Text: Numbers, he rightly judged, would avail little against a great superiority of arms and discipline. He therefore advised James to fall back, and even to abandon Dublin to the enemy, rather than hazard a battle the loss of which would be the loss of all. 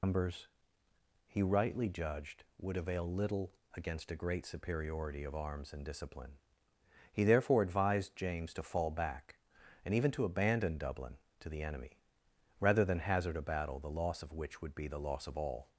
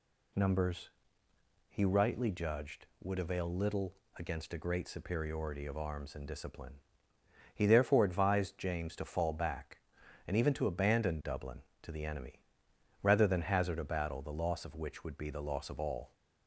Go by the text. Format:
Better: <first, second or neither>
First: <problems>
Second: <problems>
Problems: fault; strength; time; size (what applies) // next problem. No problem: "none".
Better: second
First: loses the start of "Numbers"; at 0.0 s; 105 ms // pauses between "little" and "against"; slight; at 3.5 s; 0.22 s long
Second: pauses between "little" and "against"; slight; at 3.9 s; 0.22 s long